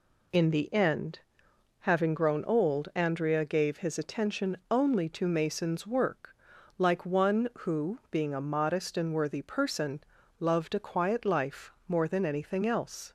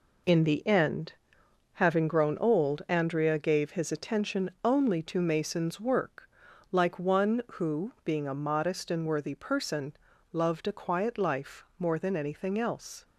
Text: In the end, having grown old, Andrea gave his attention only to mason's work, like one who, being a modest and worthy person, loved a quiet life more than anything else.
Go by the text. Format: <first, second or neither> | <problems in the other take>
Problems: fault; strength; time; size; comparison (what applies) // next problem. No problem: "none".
first | gets quieter; strong; throughout; 7.5 dB